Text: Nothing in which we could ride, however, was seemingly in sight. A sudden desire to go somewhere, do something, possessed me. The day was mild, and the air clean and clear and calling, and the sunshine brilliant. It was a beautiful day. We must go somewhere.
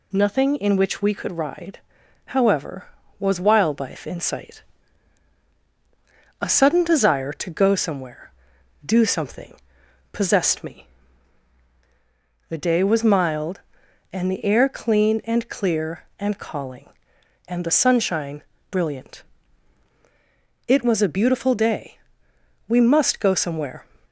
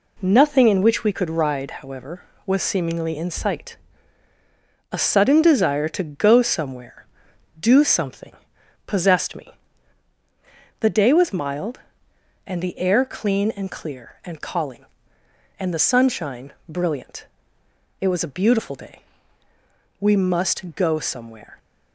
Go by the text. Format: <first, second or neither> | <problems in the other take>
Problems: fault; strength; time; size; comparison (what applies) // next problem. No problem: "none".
second | says "wildlife" for "seemingly"; at 3.4 s // pauses between "sunshine" and "brilliant"; slight; at 18.4 s; 0.28 s long; slight in the second